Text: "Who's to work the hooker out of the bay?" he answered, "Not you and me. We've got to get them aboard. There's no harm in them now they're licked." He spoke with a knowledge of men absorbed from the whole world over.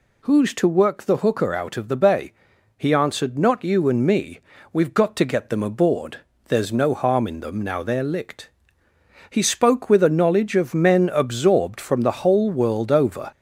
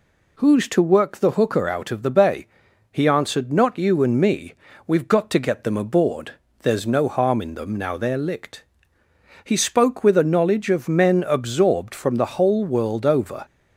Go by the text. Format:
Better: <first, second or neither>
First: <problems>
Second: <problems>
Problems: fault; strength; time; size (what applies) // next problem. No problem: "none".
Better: second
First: gets louder; slight; throughout; 3 dB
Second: none